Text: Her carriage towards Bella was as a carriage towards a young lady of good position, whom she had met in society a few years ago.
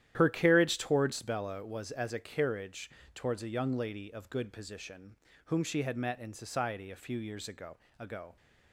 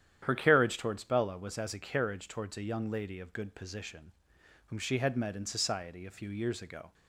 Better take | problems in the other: second | starts louder than the rest; strong; until 1.1 s; 11.5 dB; strong in the second // pauses between "carriage" and "towards"; slight; at 2.8 s; 0.24 s long // says "ago" twice; at 7.9 s

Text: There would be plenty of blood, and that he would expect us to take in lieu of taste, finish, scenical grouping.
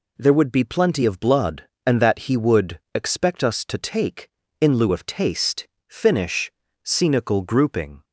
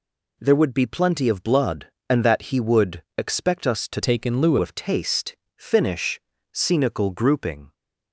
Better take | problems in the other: first | pauses between "would" and "expect"; slight; at 3.0 s; 0.16 s long; slight in the first // changes voice from "take" to "lieu"; from 4.0 to 4.5 s; 0.5 s long

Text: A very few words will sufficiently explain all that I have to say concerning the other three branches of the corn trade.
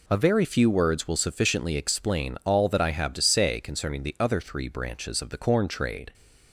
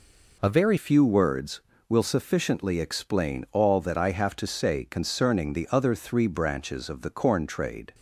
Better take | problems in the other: first | changes voice at "few"; from 0.7 s on; 7.2 s long

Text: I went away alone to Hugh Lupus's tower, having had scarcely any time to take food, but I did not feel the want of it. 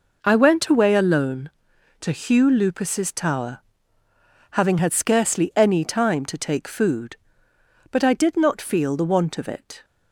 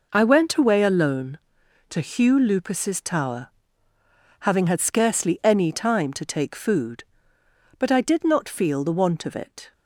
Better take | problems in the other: neither | none

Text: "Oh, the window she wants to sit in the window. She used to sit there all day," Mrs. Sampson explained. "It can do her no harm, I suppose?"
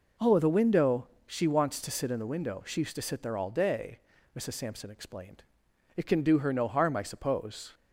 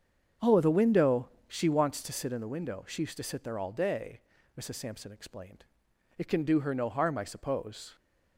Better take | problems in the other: first | starts louder than the rest; strong; until 2.1 s; 7.5 dB // pauses between "window" and "she"; slight; at 1.2 s; 0.18 s long; slight in the first

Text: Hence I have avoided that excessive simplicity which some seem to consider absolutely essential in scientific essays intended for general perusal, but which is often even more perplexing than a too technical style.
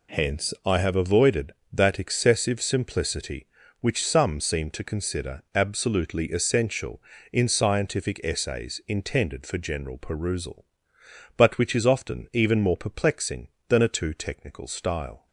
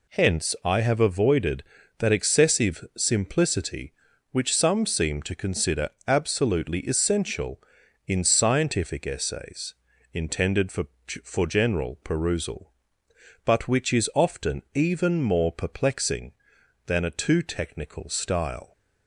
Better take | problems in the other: first | pauses between "consider" and "absolutely"; slight; at 5.8 s; 0.18 s long // pauses between "essays" and "intended"; at 9.7 s; 0.40 s long // says "for" twice; at 11.2 s

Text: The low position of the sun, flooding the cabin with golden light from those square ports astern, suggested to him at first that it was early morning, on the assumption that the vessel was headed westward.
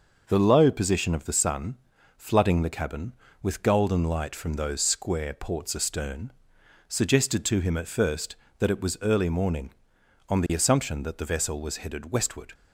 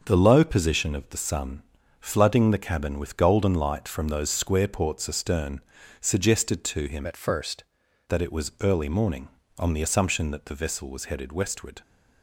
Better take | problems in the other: first | starts louder than the rest; until 1.0 s; 6 dB // changes voice from "at" to "first"; from 7.0 to 7.6 s; 0.6 s long

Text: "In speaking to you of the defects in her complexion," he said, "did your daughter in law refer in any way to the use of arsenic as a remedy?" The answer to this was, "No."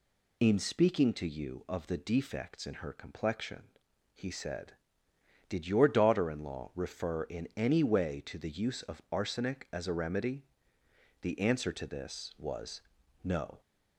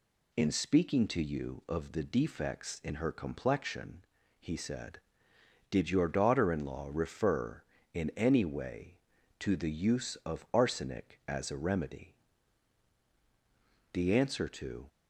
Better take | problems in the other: first | stops before "this was No"; at 14.8 s

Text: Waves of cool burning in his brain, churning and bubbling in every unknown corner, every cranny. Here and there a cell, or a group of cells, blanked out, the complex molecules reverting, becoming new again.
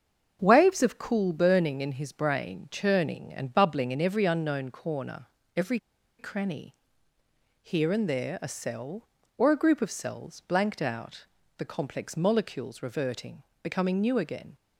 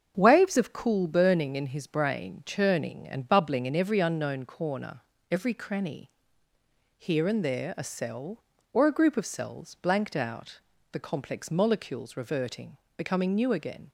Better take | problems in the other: second | starts louder than the rest; until 1.4 s; 7 dB; also in the second // pauses between "every" and "cranny"; at 5.7 s; 0.40 s long

